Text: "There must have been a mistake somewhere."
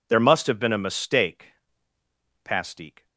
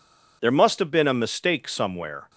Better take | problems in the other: second | says "pastique" for "somewhere"; at 2.4 s

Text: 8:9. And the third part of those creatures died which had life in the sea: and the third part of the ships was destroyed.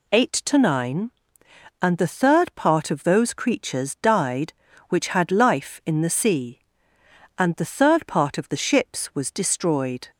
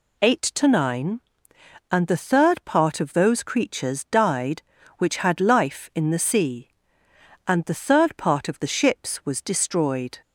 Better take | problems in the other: neither | none

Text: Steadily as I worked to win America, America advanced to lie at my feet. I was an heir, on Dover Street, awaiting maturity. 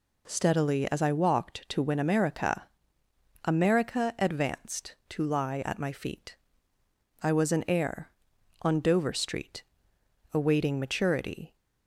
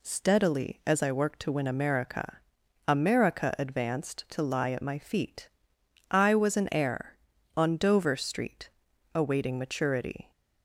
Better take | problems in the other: second | says "walked" for "worked"; at 1.1 s

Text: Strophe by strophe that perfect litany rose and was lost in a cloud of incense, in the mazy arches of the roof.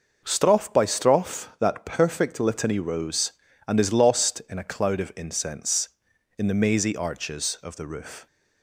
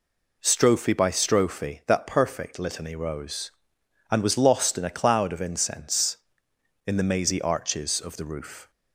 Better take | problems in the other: second | says "is" for "was"; at 3.7 s

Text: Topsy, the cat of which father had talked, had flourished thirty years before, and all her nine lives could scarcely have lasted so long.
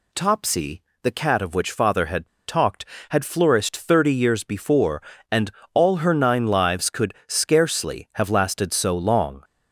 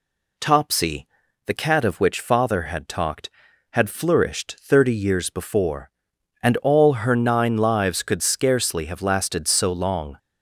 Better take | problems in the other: second | pauses between "had" and "talked"; slight; at 2.2 s; 0.19 s long // pauses between "and" and "all"; slight; at 5.4 s; 0.24 s long

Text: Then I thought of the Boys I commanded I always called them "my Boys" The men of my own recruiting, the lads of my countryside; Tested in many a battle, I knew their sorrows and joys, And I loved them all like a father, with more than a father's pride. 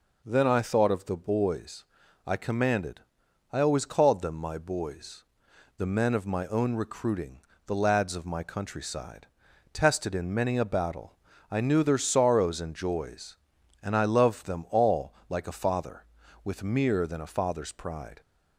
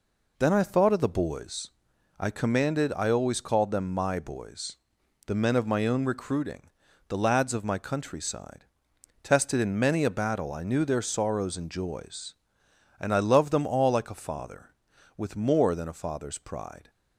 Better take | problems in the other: second | pauses between "Boys" and "I"; at 1.8 s; 0.42 s long; noticeable in the second // pauses between "commanded" and "I"; noticeable; at 3.0 s; 0.52 s long // pauses between "Boys" and "The"; noticeable; at 5.2 s; 0.54 s long; noticeable in the second // pauses between "all" and "like"; slight; at 15.1 s; 0.16 s long // says "mere" for "more"; at 16.6 s

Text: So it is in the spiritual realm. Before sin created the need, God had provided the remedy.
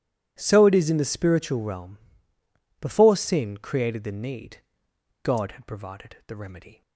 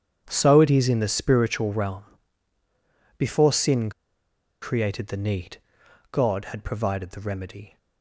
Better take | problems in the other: first | starts louder than the rest; strong; until 1.2 s; 8.5 dB // pauses between "sin" and "created"; noticeable; at 3.9 s; 0.71 s long

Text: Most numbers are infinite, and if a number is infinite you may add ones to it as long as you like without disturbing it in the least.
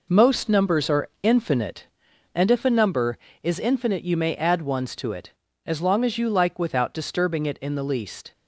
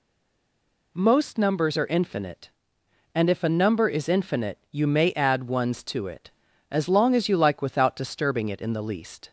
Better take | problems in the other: first | stays silent before the first word; slight; until 0.9 s; 0.9 s long

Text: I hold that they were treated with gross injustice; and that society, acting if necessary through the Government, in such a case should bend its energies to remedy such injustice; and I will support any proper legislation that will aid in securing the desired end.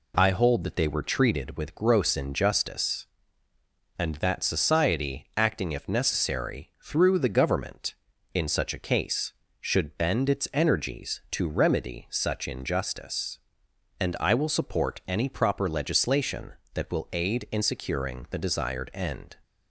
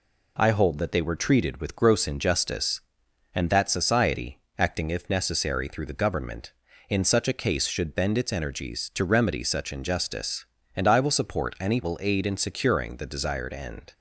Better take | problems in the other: first | skips "proper legislation that"; at 11.8 s

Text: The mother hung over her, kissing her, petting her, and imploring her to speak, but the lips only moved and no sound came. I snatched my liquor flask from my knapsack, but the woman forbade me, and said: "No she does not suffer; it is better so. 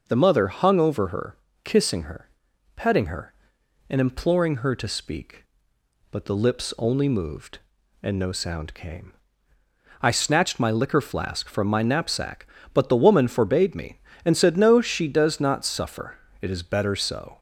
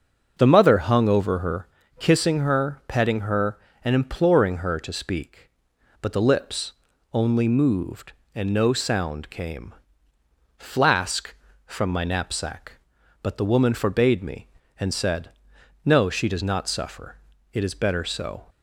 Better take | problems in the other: first | starts louder than the rest; until 1.3 s; 6.5 dB // pauses between "lips" and "only"; at 6.7 s; 0.40 s long // skips "I snatched my liquor"; at 10.1 s

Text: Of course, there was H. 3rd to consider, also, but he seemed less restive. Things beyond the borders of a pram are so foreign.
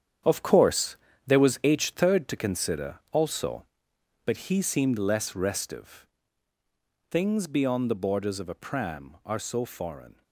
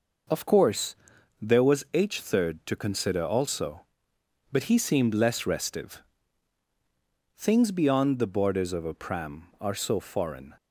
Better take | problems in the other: second | gets quieter; strong; throughout; 11.5 dB

